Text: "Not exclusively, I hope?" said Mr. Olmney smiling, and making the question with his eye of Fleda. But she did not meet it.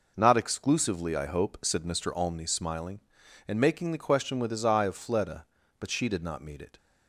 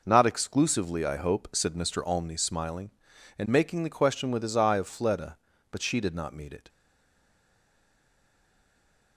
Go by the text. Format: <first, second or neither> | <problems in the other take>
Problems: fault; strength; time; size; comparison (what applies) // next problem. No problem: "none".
first | stays silent after the last word; from 6.6 s on; 2.5 s long